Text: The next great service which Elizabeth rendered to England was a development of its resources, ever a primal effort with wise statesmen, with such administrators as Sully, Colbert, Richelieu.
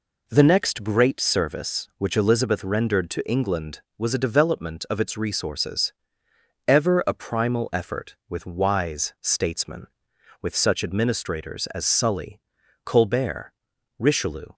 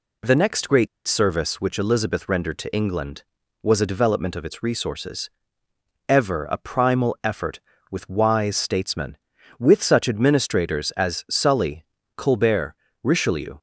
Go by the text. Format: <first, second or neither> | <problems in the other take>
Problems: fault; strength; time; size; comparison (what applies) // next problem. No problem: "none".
first | pauses between "great" and "service"; slight; at 0.8 s; 0.20 s long